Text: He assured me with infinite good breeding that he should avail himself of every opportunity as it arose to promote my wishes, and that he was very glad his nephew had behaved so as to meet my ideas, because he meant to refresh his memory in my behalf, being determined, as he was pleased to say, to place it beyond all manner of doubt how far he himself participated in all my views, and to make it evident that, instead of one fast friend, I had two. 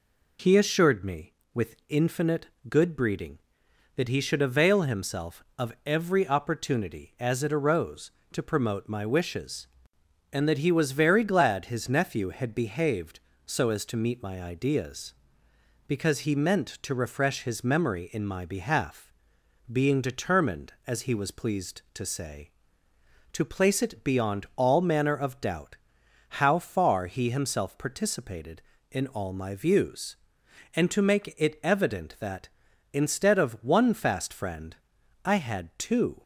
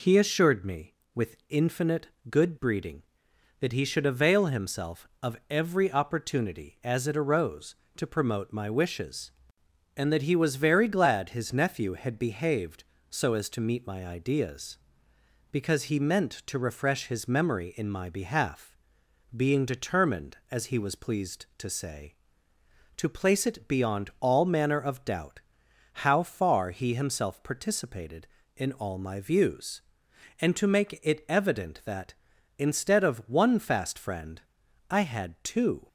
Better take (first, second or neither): neither